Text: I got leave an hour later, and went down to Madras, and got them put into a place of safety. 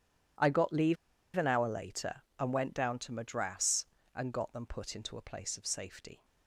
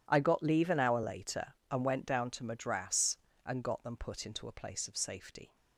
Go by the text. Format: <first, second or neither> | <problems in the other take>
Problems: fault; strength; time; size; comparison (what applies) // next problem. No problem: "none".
second | starts louder than the rest; strong; until 1.8 s; 10.5 dB; strong in the second // pauses between "leave" and "an"; at 0.9 s; 0.40 s long